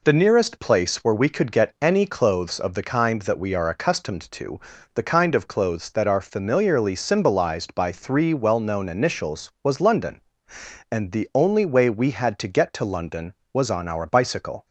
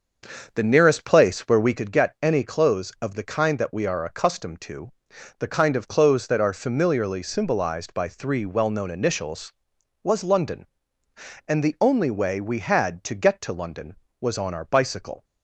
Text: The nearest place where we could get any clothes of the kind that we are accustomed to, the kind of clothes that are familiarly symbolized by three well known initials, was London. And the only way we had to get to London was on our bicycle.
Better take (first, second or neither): first